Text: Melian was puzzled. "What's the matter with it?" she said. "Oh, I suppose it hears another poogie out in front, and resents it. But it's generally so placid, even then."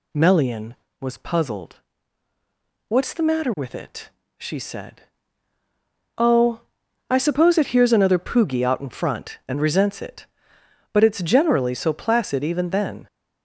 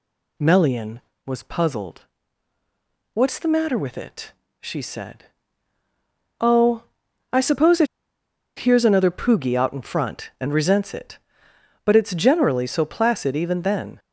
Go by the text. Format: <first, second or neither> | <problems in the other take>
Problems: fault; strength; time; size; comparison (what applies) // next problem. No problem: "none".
first | pauses between "it" and "hears"; noticeable; at 7.8 s; 0.71 s long